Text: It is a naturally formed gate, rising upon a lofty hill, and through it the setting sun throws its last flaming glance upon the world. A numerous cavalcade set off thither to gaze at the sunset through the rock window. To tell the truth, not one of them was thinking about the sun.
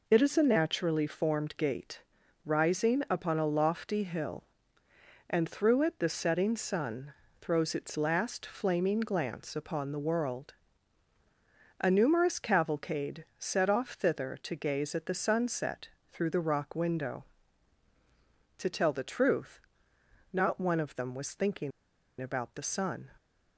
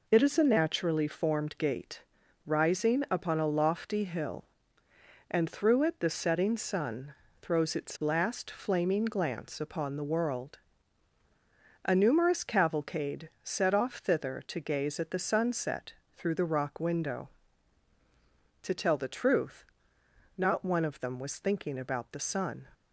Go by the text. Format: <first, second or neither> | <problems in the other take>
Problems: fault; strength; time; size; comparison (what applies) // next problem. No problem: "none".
second | pauses between "sun" and "throws"; slight; at 7.1 s; 0.28 s long; slight in the second // pauses between "cavalcade" and "set"; slight; at 13.2 s; 0.16 s long; slight in the second // pauses between "sunset" and "through"; slight; at 15.8 s; 0.24 s long; slight in the second // pauses between "thinking" and "about"; noticeable; at 21.7 s; 0.50 s long